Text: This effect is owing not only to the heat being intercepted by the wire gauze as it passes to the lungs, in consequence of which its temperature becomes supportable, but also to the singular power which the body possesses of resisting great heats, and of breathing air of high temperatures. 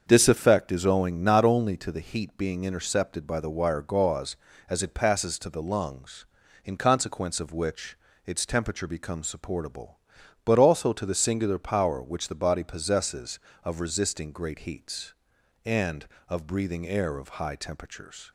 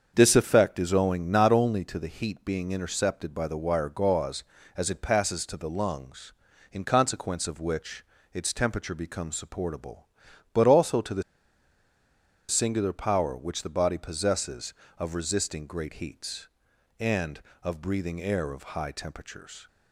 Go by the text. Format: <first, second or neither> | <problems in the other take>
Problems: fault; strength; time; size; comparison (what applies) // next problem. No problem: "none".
first | starts louder than the rest; until 1.1 s; 7 dB; also in the first // pauses between "which" and "its"; slight; at 8.0 s; 0.28 s long; slight in the first // pauses between "the" and "singular"; strong; at 11.2 s; 1.2 s long